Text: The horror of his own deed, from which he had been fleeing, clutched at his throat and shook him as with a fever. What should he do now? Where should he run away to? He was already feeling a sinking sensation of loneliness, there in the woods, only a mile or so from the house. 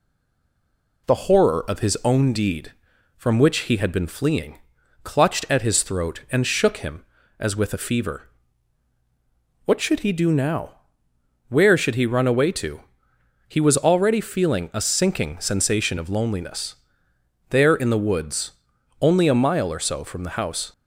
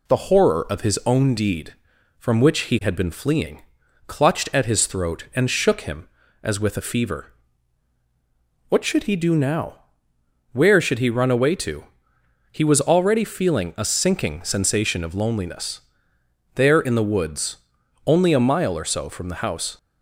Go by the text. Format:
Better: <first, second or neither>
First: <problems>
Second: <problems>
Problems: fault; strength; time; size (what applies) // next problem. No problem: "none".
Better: second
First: stays silent before the first word; until 1.0 s; 1.0 s long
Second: none